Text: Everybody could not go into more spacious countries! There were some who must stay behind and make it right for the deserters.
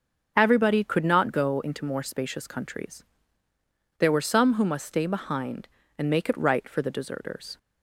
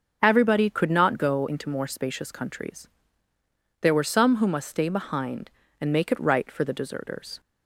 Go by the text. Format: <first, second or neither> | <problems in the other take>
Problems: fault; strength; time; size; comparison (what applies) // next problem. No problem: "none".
neither | starts louder than the rest; the same in both